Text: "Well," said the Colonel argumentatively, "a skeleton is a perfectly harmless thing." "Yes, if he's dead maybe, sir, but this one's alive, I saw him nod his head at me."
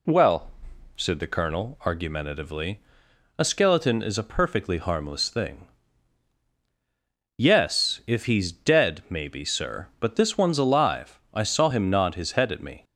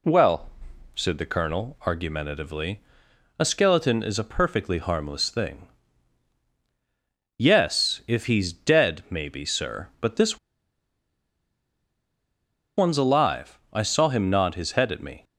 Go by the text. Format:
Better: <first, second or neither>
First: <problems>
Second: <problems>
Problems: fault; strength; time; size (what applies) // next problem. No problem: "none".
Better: first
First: none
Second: pauses between "this" and "one's"; strong; at 10.3 s; 2.4 s long